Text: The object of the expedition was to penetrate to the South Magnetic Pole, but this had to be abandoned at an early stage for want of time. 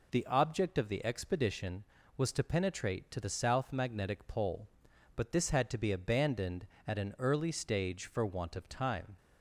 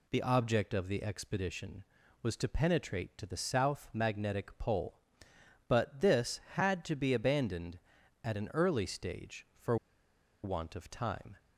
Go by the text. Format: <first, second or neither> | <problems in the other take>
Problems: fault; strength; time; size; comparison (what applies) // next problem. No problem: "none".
first | pauses between "for" and "want"; noticeable; at 9.7 s; 0.67 s long